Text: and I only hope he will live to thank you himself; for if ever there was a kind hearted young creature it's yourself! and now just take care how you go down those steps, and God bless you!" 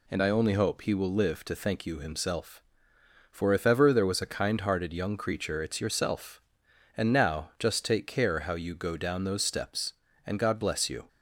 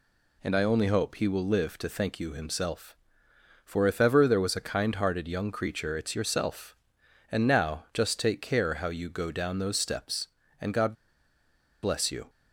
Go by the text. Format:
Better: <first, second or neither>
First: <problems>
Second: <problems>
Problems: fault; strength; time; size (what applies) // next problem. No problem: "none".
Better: first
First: none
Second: pauses between "God" and "bless"; noticeable; at 10.9 s; 0.88 s long